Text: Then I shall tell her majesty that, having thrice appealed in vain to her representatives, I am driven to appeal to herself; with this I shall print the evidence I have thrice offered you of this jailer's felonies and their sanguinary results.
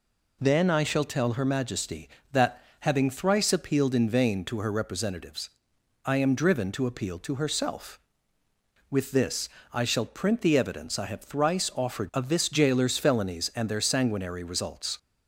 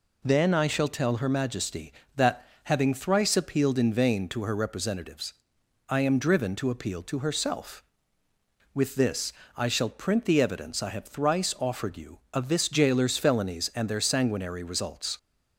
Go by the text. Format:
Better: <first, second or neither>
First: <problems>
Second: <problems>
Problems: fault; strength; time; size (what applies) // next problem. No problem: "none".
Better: second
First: pauses between "this" and "I"; slight; at 9.4 s; 0.24 s long // skips "you"; at 12.1 s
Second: pauses between "this" and "I"; slight; at 9.3 s; 0.24 s long